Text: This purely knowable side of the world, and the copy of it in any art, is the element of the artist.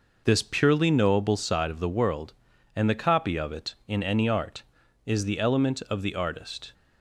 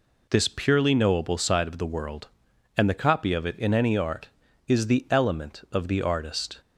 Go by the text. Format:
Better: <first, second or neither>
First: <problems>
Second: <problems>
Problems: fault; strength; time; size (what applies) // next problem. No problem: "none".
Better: second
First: starts louder than the rest; noticeable; until 1.5 s; 5.5 dB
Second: none